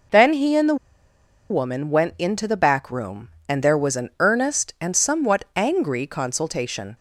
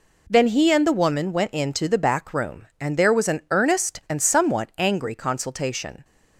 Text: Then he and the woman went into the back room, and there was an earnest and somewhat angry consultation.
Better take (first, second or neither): second